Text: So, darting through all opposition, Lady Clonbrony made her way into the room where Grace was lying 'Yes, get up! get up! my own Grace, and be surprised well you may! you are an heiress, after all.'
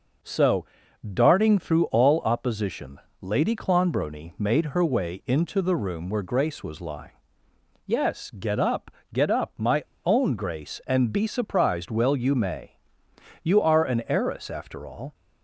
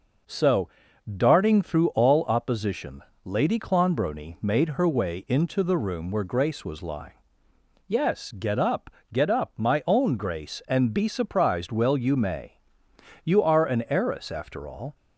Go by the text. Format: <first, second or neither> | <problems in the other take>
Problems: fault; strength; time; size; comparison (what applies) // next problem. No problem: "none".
second | pauses between "lying" and "Yes"; noticeable; at 7.1 s; 0.74 s long; noticeable in the second // pauses between "my" and "own"; slight; at 9.8 s; 0.22 s long